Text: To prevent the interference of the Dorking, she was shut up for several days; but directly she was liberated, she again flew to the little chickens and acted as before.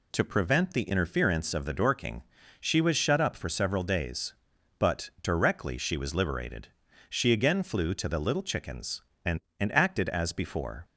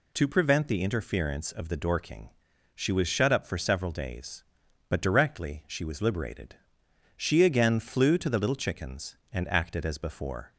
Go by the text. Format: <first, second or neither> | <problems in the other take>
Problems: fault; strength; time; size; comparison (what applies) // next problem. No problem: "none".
second | says "and" twice; at 9.6 s